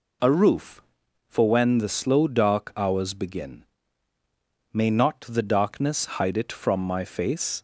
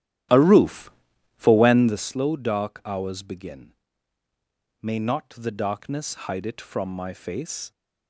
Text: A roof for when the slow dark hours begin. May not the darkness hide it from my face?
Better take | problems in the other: first | starts louder than the rest; strong; until 2.1 s; 12.5 dB

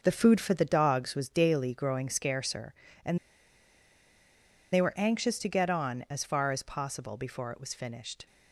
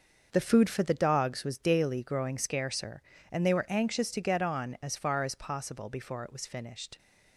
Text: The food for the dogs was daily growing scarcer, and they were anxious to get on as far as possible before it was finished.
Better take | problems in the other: second | starts louder than the rest; until 1.0 s; 6 dB; also in the second // pauses between "and" and "they"; strong; at 3.1 s; 1.5 s long

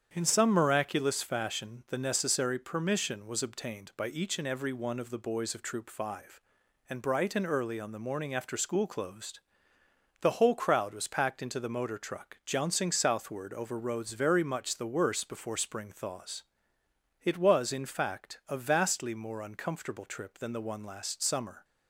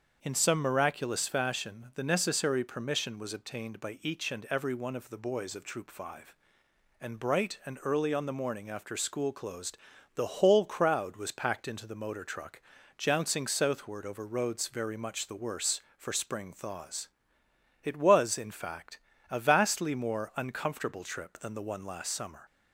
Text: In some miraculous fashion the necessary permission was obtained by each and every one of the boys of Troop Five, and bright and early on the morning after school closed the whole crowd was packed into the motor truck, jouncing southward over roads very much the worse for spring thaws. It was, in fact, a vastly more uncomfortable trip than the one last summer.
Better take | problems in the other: second | starts louder than the rest; strong; until 1.1 s; 8.5 dB; also in the second // pauses between "closed" and "the"; noticeable; at 9.3 s; 0.80 s long; also in the second // says "before" for "for"; at 15.2 s

